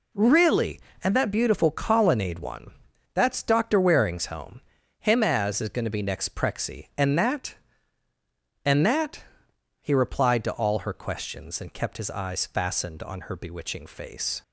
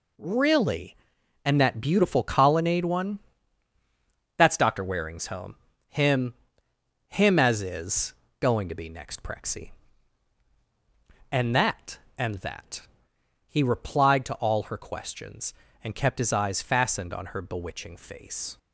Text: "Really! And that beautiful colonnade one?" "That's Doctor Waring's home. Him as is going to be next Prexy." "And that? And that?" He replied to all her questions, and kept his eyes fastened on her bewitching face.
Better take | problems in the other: first | says "Him" twice; at 7.0 s // pauses between "is" and "going"; slight; at 8.1 s; 0.26 s long

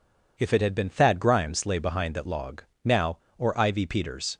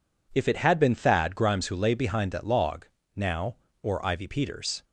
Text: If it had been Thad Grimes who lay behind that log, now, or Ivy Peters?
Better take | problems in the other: second | skips "who"; at 1.6 s

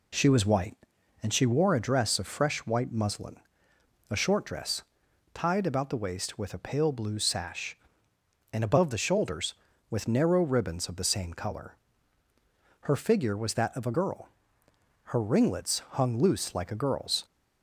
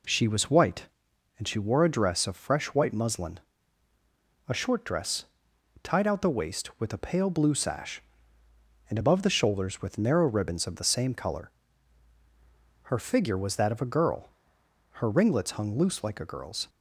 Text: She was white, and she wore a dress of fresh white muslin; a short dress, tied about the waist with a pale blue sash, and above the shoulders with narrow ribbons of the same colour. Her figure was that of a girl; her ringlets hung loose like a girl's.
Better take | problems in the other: first | says "out" for "about"; at 6.0 s

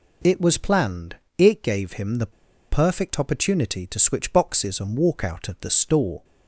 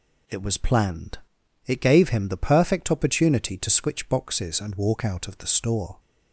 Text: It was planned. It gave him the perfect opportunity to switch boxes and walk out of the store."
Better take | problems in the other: second | pauses between "the" and "perfect"; at 2.3 s; 0.40 s long

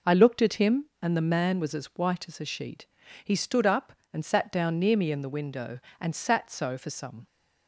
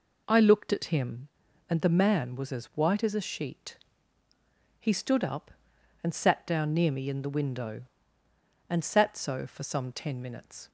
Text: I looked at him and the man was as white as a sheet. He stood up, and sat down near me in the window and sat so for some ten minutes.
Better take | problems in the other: second | stops before "ten minutes"; at 7.2 s

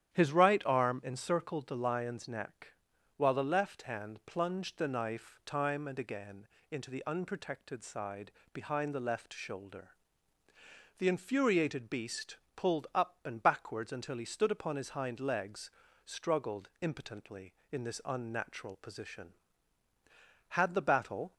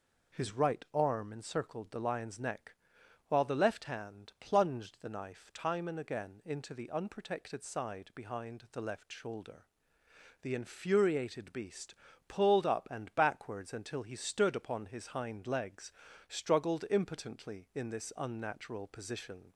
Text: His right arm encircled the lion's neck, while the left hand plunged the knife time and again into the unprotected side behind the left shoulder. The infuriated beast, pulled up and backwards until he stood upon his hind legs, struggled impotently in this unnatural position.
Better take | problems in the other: second | starts louder than the rest; strong; until 1.2 s; 10.5 dB // pauses between "again" and "into"; slight; at 6.4 s; 0.24 s long // pauses between "side" and "behind"; slight; at 8.3 s; 0.20 s long // goes on to say "Had the battle"; noticeable; from 20.4 s on; 0.84 s long

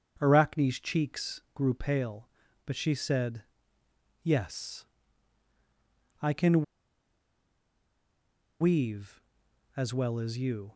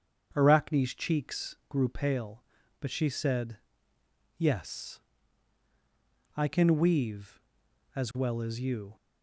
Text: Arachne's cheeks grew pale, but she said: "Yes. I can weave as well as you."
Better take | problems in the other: second | starts louder than the rest; strong; until 1.2 s; 7 dB; strong in the second // pauses between "can" and "weave"; strong; at 6.6 s; 1.9 s long

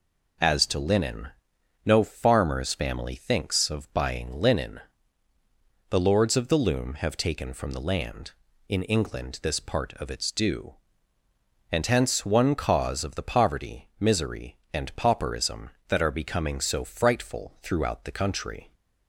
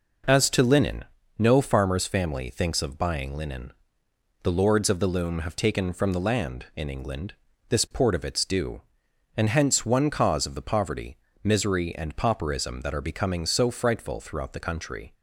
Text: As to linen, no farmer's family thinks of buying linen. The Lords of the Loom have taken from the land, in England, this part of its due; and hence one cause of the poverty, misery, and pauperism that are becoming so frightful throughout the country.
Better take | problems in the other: first | says "port" for "part"; at 7.9 s

